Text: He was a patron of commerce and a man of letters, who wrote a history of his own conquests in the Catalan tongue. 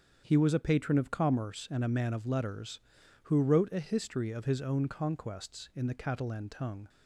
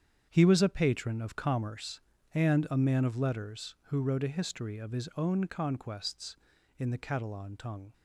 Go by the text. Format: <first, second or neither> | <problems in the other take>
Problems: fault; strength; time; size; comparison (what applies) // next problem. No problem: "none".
first | gets quieter; strong; throughout; 11.5 dB // starts louder than the rest; strong; until 1.3 s; 8 dB; strong in the first